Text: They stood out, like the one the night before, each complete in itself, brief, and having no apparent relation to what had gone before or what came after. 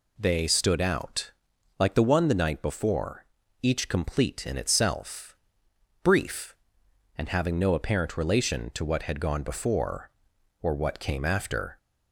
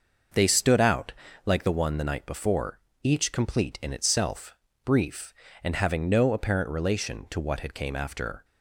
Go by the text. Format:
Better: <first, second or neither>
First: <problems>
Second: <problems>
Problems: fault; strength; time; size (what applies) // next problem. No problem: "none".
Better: first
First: none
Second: skips "gone before or what"; at 7.7 s